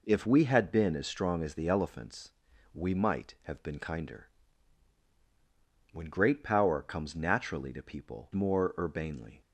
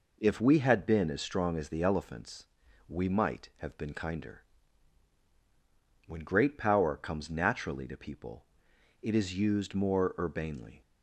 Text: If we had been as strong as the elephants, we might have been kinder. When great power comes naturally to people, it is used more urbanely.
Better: second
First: skips "it is used"; at 8.3 s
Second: none

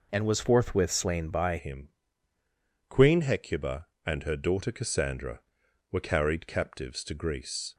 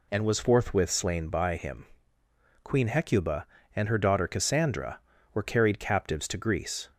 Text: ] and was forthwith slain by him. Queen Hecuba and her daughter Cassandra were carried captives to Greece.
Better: second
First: changes voice at "him"; from 1.5 s on; 6.2 s long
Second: none

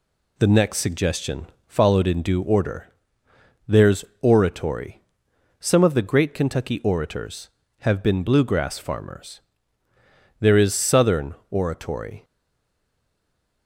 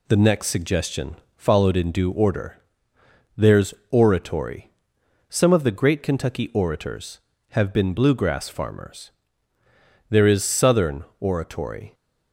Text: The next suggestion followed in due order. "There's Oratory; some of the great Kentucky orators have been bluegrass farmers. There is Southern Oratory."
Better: second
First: pauses between "suggestion" and "followed"; slight; at 1.4 s; 0.20 s long // pauses between "There's" and "Oratory"; slight; at 4.0 s; 0.16 s long // pauses between "Southern" and "Oratory"; slight; at 11.3 s; 0.16 s long // stays silent after the last word; noticeable; from 12.2 s on; 1.4 s long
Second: pauses between "suggestion" and "followed"; slight; at 1.1 s; 0.20 s long // pauses between "There's" and "Oratory"; slight; at 3.7 s; 0.16 s long // pauses between "Southern" and "Oratory"; slight; at 11.0 s; 0.16 s long

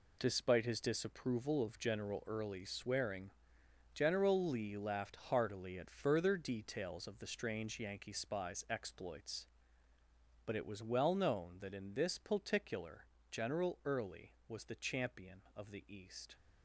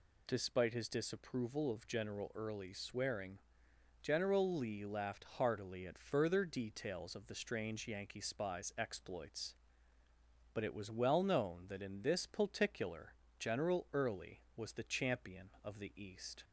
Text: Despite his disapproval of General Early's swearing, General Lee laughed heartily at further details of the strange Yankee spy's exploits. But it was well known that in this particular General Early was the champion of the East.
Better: second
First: gets quieter; strong; throughout; 9.5 dB // pauses between "particular" and "General"; slight; at 13.0 s; 0.24 s long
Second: pauses between "particular" and "General"; slight; at 13.1 s; 0.24 s long

